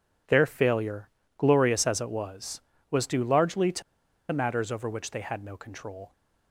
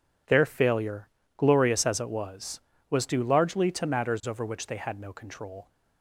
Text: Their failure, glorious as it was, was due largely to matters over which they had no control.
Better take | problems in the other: second | pauses between "to" and "matters"; noticeable; at 3.8 s; 0.49 s long

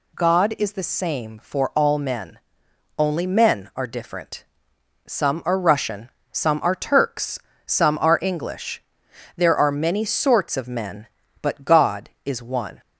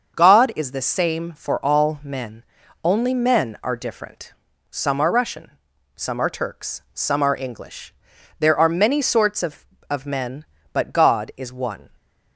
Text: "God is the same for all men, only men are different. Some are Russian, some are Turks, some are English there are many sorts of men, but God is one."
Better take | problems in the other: first | starts louder than the rest; until 1.1 s; 6.5 dB // pauses between "English" and "there"; noticeable; at 7.9 s; 0.46 s long; noticeable in the first // says "of" twice; at 9.8 s

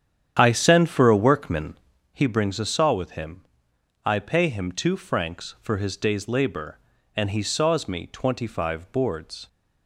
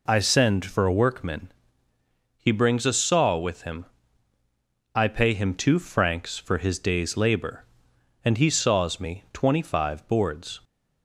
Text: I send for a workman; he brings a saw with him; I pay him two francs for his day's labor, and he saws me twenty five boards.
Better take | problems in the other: second | starts louder than the rest; strong; until 2.2 s; 9.5 dB

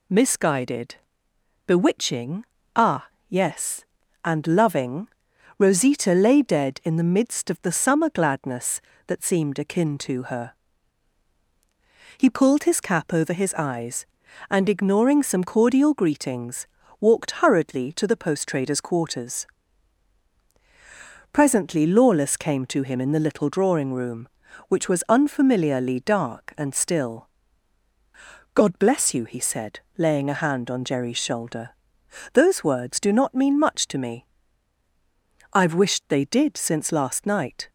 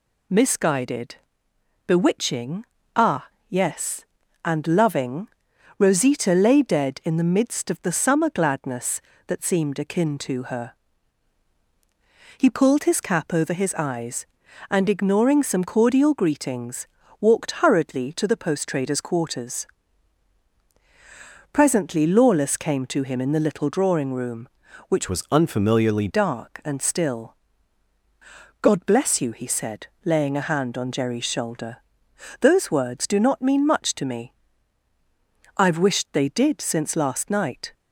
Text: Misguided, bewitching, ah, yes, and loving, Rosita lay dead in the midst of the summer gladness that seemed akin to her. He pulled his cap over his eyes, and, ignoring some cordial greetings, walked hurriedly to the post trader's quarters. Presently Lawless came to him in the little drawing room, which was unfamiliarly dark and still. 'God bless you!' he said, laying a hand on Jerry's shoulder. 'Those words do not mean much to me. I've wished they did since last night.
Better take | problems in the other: first | changes voice from "was" to "unfamiliarly"; from 25.0 to 26.0 s; 1.0 s long

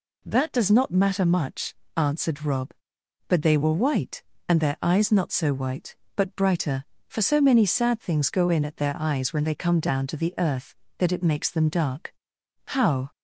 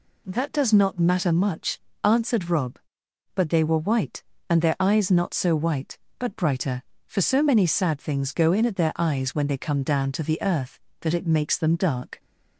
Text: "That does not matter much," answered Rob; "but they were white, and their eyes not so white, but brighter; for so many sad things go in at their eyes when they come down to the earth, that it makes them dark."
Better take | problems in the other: second | goes on to say "How"; slight; from 12.6 s on; 0.44 s long

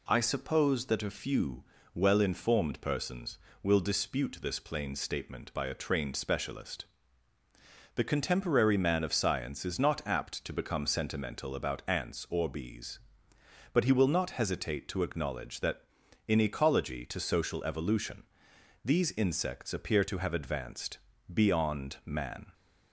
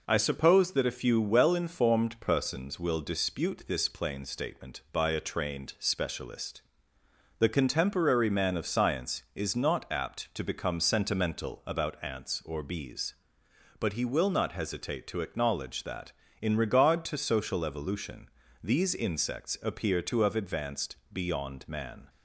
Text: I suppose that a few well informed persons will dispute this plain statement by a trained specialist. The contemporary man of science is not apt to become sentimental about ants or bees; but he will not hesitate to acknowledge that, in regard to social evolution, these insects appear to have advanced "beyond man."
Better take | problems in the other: second | pauses between "few" and "well"; slight; at 1.6 s; 0.30 s long // says "ecology" for "regard"; at 16.3 s // pauses between "advanced" and "beyond"; slight; at 20.9 s; 0.34 s long; slight in the second

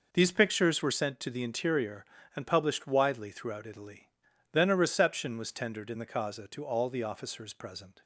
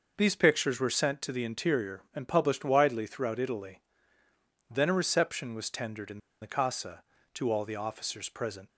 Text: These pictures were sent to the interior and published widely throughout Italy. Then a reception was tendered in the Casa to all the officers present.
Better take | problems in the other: first | pauses between "in" and "the"; slight; at 6.1 s; 0.23 s long

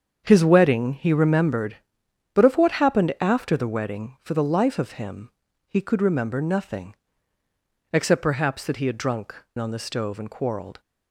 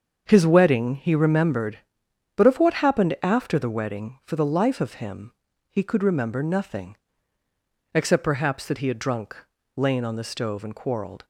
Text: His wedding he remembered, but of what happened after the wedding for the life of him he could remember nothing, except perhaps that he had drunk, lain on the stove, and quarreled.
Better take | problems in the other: second | starts louder than the rest; strong; until 1.2 s; 7 dB; also in the second // pauses between "him" and "he"; at 5.2 s; 0.38 s long; also in the second // skips "lain"; at 9.4 s

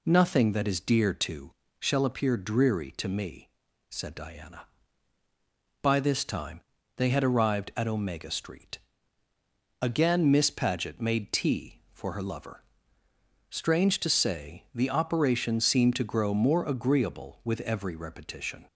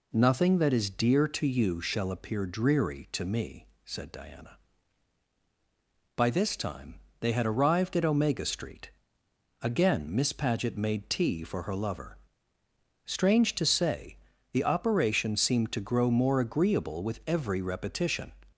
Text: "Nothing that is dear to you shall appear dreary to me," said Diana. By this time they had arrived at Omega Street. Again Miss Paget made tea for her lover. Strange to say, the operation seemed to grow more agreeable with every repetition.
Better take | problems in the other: second | skips "you"; at 1.6 s // pauses between "time" and "they"; at 6.5 s; 0.38 s long; slight in the second

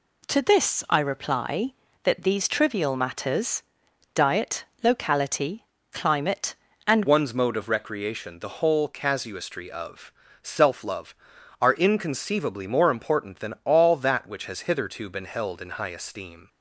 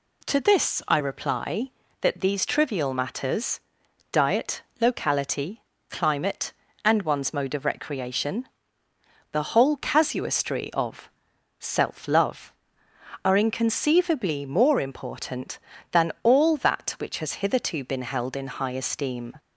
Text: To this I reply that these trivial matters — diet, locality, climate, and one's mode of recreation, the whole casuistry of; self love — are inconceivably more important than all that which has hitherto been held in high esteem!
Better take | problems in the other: second | changes voice at "one's"; from 7.0 s on; 9.4 s long

